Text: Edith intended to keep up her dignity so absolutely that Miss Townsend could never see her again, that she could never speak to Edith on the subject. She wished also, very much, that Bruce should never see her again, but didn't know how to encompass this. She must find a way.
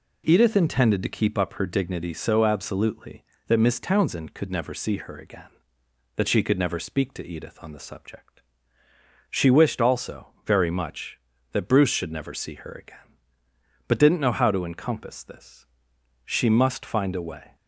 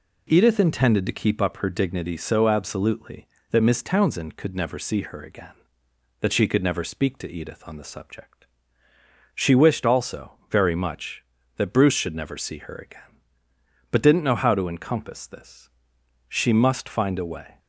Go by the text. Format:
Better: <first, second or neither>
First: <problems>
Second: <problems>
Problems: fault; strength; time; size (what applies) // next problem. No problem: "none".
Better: neither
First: none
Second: none